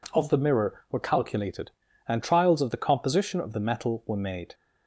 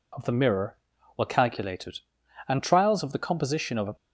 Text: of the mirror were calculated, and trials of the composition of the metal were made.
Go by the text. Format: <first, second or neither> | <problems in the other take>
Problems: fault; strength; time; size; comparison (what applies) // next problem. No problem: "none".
first | stops before "the metal were made"; at 3.9 s